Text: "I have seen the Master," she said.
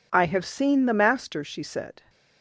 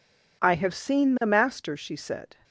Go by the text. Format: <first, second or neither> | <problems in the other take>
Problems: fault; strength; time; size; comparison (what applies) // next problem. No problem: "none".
neither | none